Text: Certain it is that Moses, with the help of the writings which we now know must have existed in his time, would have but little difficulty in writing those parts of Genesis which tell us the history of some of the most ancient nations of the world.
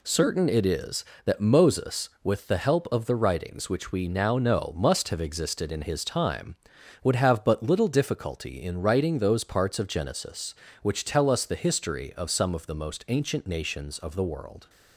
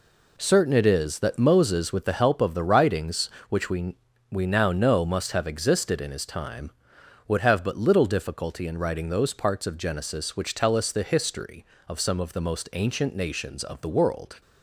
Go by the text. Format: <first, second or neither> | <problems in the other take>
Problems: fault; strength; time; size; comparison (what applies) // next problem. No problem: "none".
first | says "we" twice; at 4.3 s